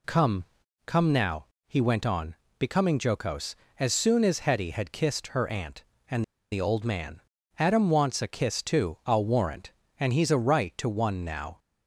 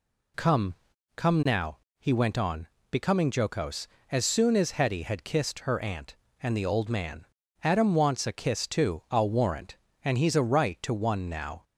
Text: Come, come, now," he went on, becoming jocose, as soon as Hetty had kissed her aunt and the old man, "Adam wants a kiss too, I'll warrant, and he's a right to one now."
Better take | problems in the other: second | pauses between "and" and "the"; slight; at 6.2 s; 0.28 s long

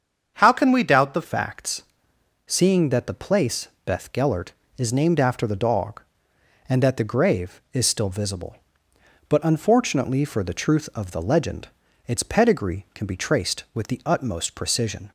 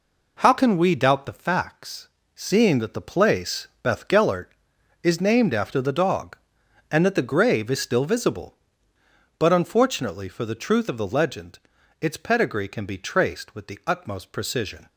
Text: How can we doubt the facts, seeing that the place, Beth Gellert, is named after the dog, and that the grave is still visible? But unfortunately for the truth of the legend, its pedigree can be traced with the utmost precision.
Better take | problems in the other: second | starts louder than the rest; until 1.4 s; 7 dB // changes voice at "facts"; from 1.2 s on; 13.8 s long

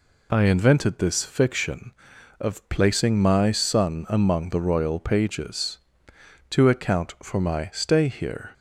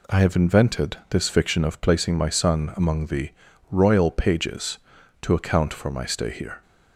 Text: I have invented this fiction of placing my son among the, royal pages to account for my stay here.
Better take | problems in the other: second | skips "have"; at 0.4 s

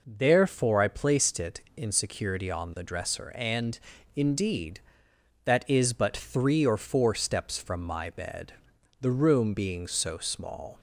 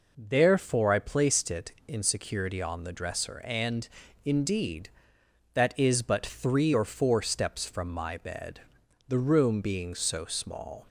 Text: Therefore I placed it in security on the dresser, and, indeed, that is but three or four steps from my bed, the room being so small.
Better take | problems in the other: neither | none

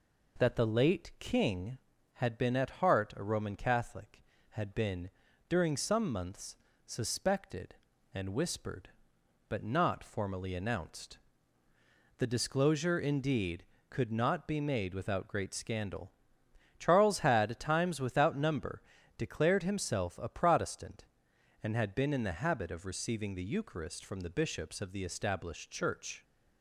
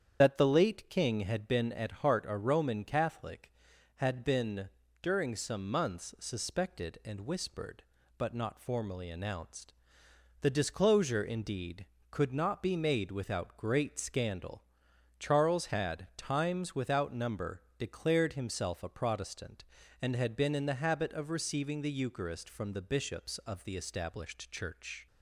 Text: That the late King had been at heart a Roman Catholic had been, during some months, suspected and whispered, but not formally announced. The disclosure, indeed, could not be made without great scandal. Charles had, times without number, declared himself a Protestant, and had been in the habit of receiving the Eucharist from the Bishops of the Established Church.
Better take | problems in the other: first | loses the start of "That"; at 0.2 s; 35 ms // starts louder than the rest; strong; until 1.2 s; 8.5 dB

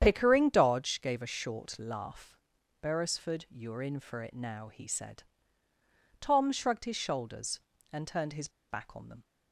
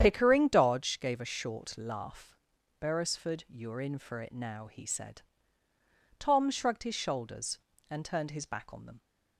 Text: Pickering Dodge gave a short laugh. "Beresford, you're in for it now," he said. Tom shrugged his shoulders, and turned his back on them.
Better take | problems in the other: second | starts louder than the rest; strong; until 1.0 s; 9 dB; strong in the second // pauses between "his" and "back"; slight; at 8.4 s; 0.21 s long

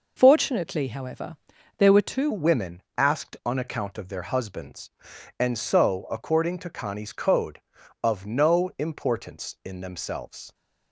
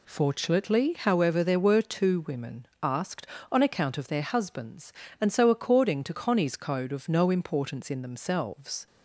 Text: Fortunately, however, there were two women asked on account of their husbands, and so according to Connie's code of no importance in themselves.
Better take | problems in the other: second | changes voice at "women"; from 2.3 s on; 8.2 s long // pauses between "women" and "asked"; slight; at 2.8 s; 0.16 s long

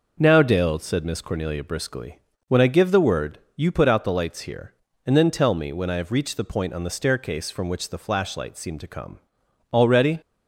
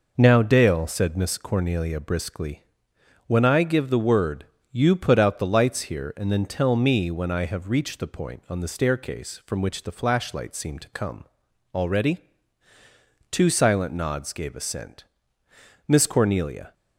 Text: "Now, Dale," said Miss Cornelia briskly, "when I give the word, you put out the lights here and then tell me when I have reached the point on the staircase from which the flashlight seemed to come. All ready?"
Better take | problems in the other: first | goes on to say "Two silent nods gave assent Miss Cornelia"; strong; from 13.3 s on; 3.4 s long

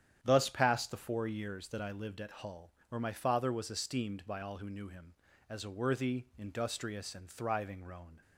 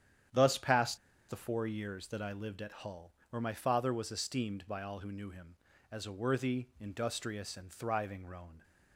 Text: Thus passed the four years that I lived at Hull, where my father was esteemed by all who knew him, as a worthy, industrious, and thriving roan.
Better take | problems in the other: first | starts louder than the rest; strong; until 1.6 s; 9.5 dB; strong in the first // pauses between "passed" and "the"; slight; at 0.9 s; 0.32 s long

